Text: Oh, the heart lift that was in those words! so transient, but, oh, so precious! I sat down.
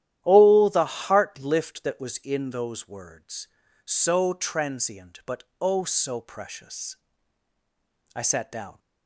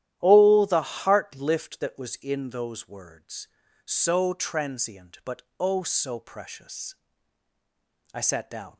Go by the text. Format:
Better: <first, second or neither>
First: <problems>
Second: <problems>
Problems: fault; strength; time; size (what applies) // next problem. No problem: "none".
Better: neither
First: starts louder than the rest; strong; until 1.2 s; 11.5 dB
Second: starts louder than the rest; strong; until 1.2 s; 11.5 dB